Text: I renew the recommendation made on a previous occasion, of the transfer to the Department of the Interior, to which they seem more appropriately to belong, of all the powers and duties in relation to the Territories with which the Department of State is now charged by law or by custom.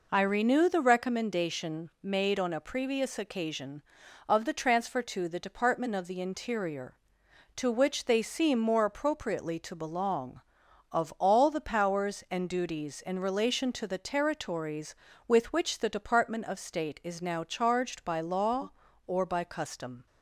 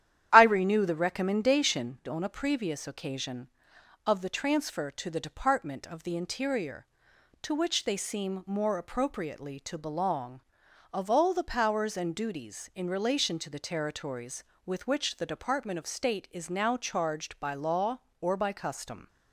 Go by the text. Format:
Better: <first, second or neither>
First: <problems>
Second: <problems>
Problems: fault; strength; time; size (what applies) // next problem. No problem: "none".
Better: first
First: none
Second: starts louder than the rest; strong; until 1.3 s; 11 dB // skips "made"; at 2.0 s